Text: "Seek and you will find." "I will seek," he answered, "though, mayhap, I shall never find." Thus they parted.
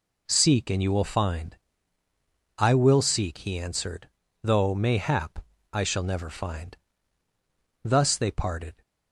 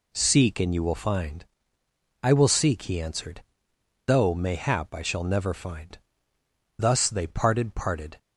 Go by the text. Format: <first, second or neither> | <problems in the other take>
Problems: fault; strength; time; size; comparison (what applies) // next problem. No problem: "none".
first | says "parted" twice; at 7.7 s